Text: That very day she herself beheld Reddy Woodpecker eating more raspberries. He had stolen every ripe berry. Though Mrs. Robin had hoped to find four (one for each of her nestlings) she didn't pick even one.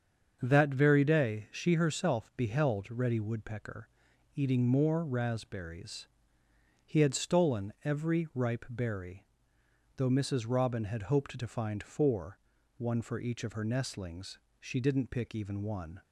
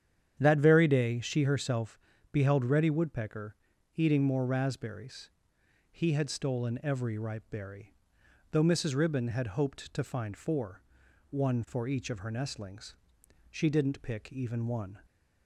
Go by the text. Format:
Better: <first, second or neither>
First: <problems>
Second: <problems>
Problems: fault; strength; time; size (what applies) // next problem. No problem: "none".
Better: first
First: starts louder than the rest; until 1.4 s; 7 dB // pauses between "Woodpecker" and "eating"; noticeable; at 3.8 s; 0.48 s long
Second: starts louder than the rest; strong; until 1.3 s; 9.5 dB // pauses between "herself" and "beheld"; slight; at 1.9 s; 0.32 s long // pauses between "Woodpecker" and "eating"; at 3.5 s; 0.40 s long // says "Ribbon" for "Robin"; at 8.9 s